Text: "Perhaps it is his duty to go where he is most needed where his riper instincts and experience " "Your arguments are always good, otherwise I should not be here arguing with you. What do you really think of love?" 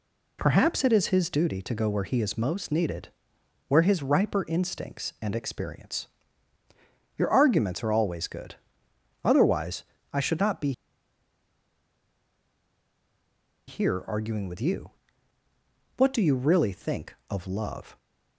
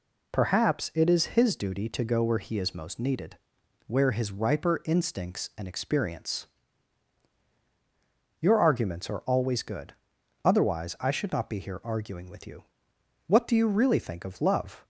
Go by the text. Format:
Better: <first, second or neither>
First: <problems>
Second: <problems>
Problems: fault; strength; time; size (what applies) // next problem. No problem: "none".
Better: second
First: pauses between "needed" and "where"; noticeable; at 3.0 s; 0.58 s long // pauses between "otherwise" and "I"; slight; at 9.8 s; 0.30 s long // pauses between "be" and "here"; strong; at 10.7 s; 2.9 s long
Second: pauses between "needed" and "where"; noticeable; at 3.3 s; 0.50 s long